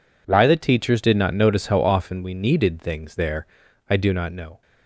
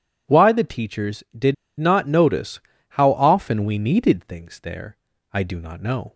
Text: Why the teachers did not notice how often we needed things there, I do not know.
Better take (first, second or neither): first